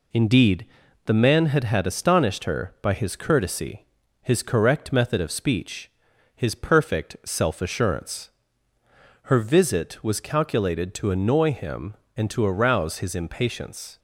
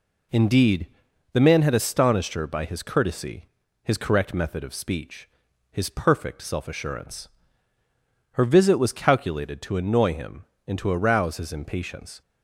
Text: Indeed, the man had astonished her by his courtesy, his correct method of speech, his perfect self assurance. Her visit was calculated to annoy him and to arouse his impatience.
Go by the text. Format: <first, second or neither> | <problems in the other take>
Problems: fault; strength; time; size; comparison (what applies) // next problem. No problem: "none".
second | says "had" twice; at 1.6 s